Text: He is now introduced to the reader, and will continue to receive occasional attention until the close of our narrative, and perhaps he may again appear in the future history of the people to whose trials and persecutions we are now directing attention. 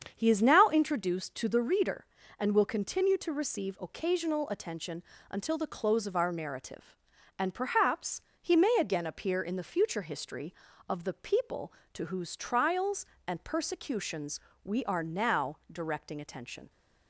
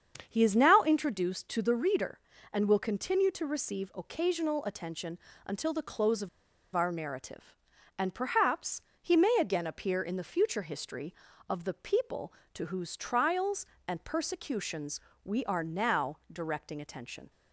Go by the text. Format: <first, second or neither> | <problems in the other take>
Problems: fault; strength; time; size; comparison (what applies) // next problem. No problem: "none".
first | starts louder than the rest; strong; until 1.2 s; 7.5 dB; strong in the first // pauses between "attention" and "until"; slight; at 5.1 s; 0.28 s long; slight in the first // pauses between "of" and "our"; noticeable; at 6.2 s; 0.47 s long // pauses between "perhaps" and "he"; slight; at 8.8 s; 0.18 s long; slight in the first // pauses between "persecutions" and "we"; slight; at 14.9 s; 0.24 s long; slight in the first